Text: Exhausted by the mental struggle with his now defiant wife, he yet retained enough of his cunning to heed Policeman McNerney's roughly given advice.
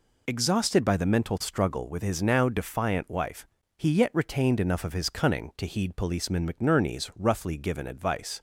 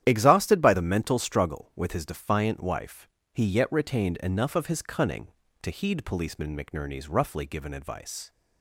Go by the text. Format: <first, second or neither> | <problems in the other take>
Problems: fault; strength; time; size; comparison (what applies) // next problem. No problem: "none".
first | starts louder than the rest; strong; until 1.0 s; 11 dB // skips "now"; at 2.0 s